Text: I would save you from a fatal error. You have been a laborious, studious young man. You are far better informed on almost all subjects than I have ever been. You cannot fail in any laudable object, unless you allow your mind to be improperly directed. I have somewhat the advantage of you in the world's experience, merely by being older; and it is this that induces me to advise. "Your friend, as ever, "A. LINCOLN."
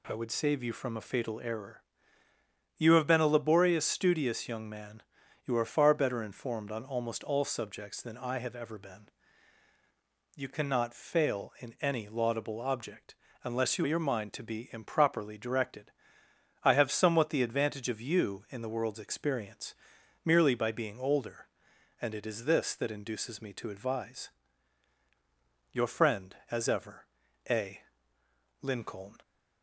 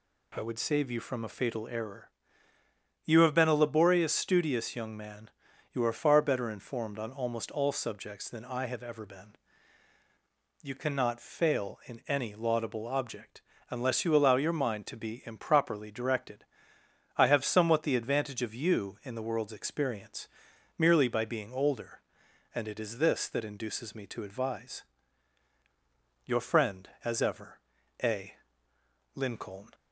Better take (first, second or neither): second